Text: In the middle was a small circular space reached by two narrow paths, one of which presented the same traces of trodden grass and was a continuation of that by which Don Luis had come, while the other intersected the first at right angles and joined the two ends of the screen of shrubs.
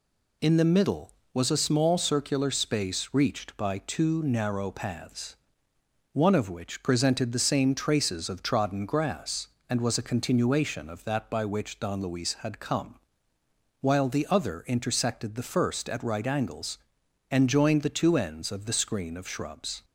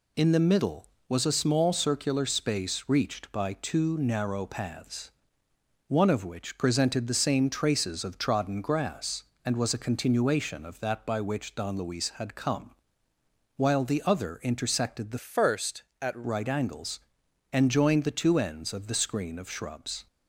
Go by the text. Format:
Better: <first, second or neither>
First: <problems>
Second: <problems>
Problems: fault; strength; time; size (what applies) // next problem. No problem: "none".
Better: first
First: none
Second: changes voice from "first" to "at"; from 15.1 to 16.2 s; 1.1 s long